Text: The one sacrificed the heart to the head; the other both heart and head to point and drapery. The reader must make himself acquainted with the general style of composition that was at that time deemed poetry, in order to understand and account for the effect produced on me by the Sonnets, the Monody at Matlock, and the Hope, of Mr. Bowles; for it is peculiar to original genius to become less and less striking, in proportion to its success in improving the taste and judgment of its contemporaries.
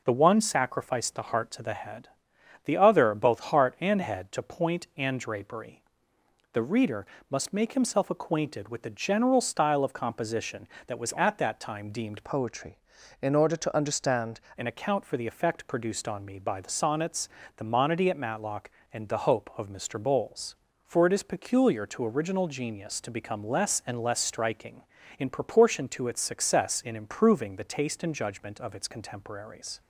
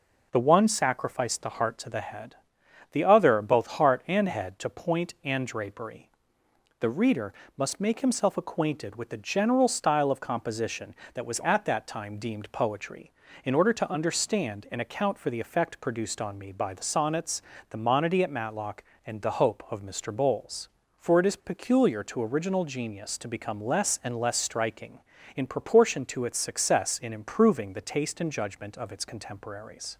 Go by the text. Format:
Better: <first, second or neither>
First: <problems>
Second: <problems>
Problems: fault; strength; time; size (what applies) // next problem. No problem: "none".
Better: second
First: pauses between "reader" and "must"; slight; at 7.0 s; 0.24 s long // changes voice from "poetry" to "understand"; from 12.2 to 14.4 s; 2.2 s long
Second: pauses between "reader" and "must"; slight; at 7.3 s; 0.24 s long